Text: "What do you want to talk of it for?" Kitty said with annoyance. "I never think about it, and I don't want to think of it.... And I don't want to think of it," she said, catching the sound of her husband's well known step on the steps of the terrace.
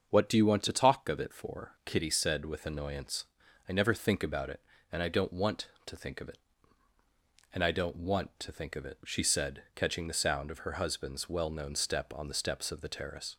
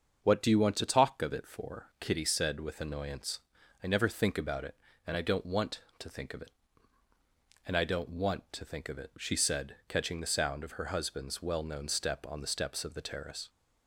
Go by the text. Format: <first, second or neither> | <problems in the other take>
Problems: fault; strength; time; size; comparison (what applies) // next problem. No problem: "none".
neither | starts louder than the rest; the same in both